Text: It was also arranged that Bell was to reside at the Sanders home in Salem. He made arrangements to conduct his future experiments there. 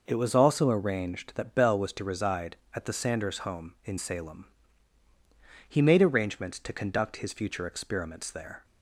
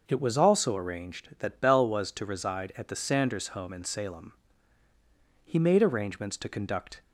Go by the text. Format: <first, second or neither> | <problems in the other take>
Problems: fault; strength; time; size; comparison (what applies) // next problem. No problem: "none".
first | stops before "his future experiments there"; at 7.0 s